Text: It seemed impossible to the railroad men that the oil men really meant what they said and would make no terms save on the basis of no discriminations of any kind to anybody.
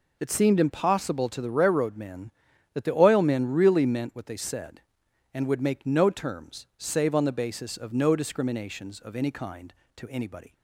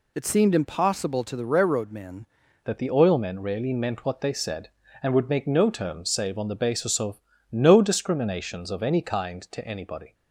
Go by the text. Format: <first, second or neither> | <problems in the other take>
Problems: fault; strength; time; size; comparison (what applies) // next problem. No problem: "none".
first | changes voice at "that"; from 2.6 s on; 7.5 s long // pauses between "of" and "no"; slight; at 7.1 s; 0.32 s long